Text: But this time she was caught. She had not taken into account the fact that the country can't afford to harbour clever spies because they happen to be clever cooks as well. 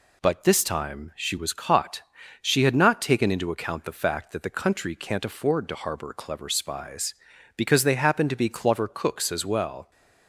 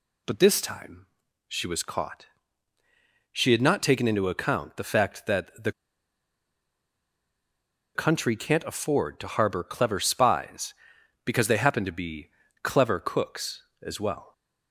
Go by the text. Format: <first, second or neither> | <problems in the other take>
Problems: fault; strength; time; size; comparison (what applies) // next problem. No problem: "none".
first | pauses between "time" and "she"; at 1.0 s; 0.42 s long // pauses between "the" and "country"; strong; at 5.7 s; 2.2 s long // pauses between "be" and "clever"; slight; at 12.2 s; 0.34 s long